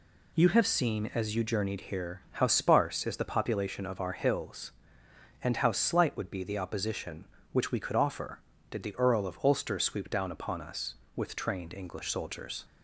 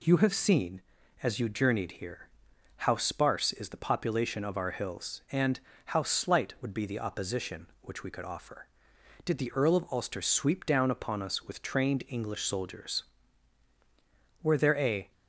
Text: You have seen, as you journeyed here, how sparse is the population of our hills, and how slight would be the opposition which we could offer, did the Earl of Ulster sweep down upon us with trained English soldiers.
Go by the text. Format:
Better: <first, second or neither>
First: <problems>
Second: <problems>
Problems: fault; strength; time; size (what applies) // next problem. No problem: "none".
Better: first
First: none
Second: pauses between "and" and "how"; slight; at 5.6 s; 0.26 s long // goes on to say "Were there a"; noticeable; from 14.4 s on; 0.70 s long